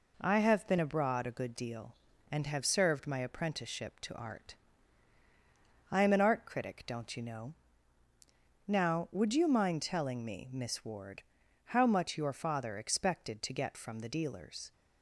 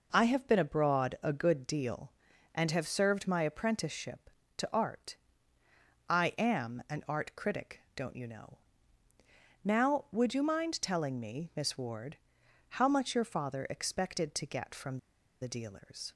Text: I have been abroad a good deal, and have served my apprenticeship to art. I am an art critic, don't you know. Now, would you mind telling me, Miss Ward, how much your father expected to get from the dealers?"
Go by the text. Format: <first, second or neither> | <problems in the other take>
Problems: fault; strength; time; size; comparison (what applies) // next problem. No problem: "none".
first | pauses between "from" and "the"; at 14.9 s; 0.44 s long